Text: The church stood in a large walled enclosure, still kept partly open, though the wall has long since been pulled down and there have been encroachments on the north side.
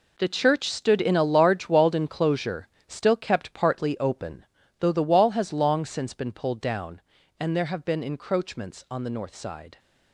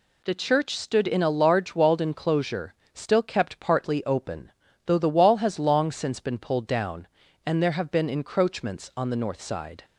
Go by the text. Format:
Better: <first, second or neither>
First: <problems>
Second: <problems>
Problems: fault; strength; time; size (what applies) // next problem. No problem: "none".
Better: second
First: gets quieter; strong; throughout; 11.5 dB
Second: none